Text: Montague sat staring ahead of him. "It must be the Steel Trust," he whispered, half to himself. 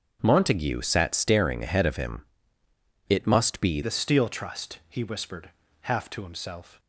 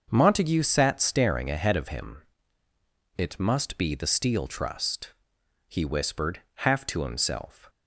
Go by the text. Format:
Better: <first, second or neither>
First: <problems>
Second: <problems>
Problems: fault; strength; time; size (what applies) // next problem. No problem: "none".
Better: second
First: starts louder than the rest; until 1.2 s; 6.5 dB // changes voice at "the"; from 3.8 s on; 2.9 s long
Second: starts louder than the rest; until 1.1 s; 6.5 dB